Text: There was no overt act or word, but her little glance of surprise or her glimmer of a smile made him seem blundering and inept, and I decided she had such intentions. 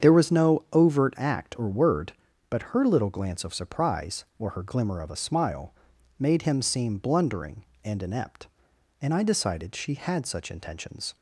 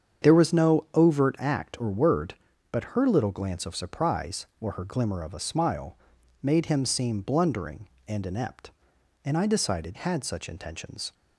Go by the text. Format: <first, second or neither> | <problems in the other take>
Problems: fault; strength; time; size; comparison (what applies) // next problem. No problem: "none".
first | starts louder than the rest; strong; until 1.3 s; 8 dB; strong in the first // pauses between "smile" and "made"; at 5.9 s; 0.44 s long; also in the first // skips "she"; at 9.9 s